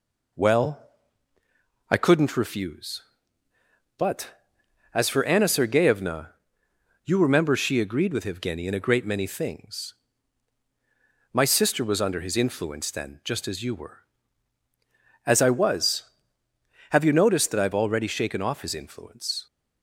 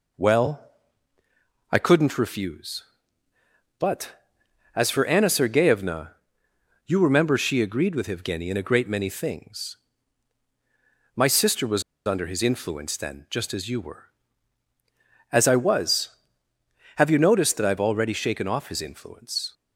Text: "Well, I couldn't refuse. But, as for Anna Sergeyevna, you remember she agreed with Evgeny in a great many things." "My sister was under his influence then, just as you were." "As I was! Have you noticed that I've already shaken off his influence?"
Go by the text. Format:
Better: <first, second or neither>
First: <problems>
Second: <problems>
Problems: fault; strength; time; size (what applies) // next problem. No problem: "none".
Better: first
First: none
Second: pauses between "was" and "under"; slight; at 11.8 s; 0.24 s long